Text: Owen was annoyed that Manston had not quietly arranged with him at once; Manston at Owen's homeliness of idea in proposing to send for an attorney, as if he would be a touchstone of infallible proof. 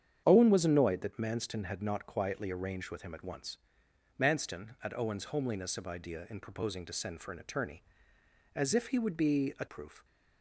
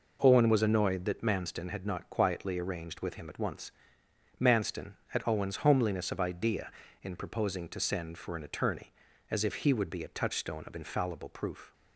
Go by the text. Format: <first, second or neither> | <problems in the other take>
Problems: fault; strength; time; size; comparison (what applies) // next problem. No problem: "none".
second | starts louder than the rest; strong; until 1.2 s; 8.5 dB // skips "touchstone of infallible"; at 9.6 s